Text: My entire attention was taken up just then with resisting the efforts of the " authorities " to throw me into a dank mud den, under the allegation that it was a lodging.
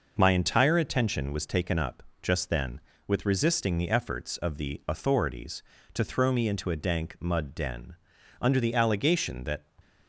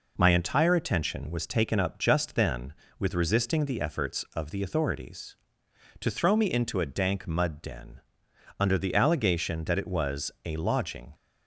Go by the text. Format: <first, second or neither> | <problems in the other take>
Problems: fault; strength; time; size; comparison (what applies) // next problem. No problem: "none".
second | pauses between "up" and "just"; slight; at 2.0 s; 0.22 s long // stops before "it was a lodging"; at 9.8 s